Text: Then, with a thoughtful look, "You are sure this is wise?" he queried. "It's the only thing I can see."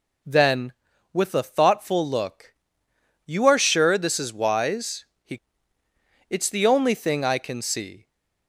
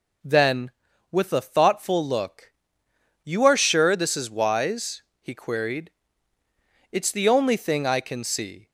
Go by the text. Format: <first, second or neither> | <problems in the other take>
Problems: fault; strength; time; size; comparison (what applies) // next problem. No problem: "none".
second | skips "queried"; at 5.8 s